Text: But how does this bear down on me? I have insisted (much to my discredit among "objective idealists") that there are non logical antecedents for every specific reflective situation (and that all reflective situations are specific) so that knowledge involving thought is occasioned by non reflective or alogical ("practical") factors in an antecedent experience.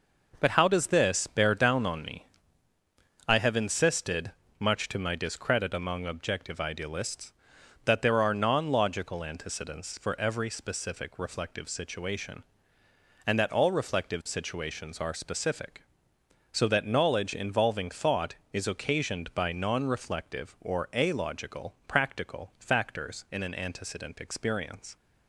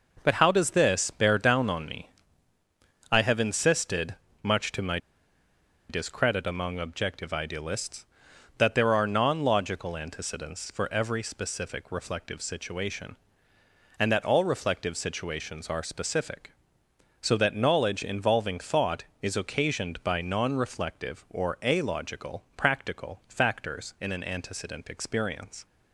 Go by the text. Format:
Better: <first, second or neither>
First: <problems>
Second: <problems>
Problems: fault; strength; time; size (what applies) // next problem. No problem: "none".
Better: first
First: none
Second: pauses between "my" and "discredit"; noticeable; at 4.9 s; 0.91 s long